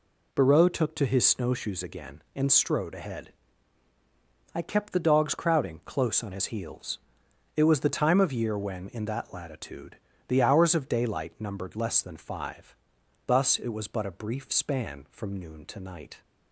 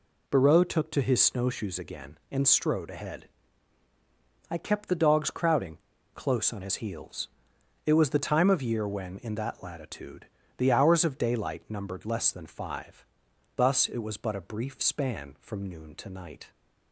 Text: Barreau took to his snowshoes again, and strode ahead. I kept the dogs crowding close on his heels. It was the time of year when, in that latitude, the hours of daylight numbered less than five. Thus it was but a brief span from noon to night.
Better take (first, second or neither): first